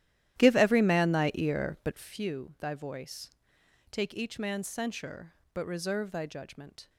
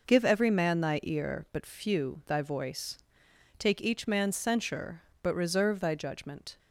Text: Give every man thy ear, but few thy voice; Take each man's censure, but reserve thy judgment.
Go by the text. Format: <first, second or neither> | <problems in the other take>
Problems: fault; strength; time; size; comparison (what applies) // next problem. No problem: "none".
second | starts louder than the rest; strong; until 2.2 s; 12.5 dB